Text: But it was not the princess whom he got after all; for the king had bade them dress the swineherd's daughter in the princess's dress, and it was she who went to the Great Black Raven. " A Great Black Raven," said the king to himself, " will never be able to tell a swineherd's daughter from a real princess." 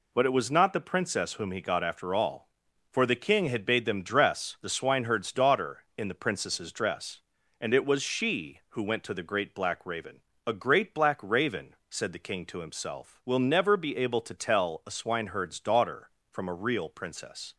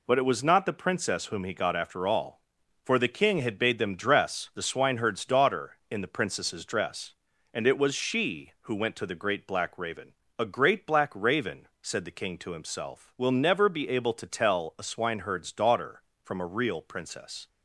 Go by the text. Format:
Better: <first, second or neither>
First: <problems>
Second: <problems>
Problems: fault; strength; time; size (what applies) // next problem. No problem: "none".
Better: neither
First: none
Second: none